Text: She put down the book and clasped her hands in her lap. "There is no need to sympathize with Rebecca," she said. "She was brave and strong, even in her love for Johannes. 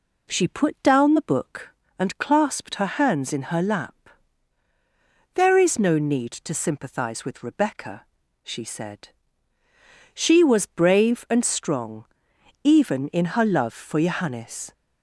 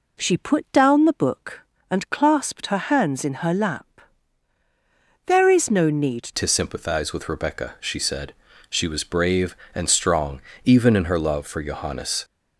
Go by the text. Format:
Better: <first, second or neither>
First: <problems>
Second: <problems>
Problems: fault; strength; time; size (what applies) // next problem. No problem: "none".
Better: first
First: none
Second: changes voice at "to"; from 6.3 s on; 5.9 s long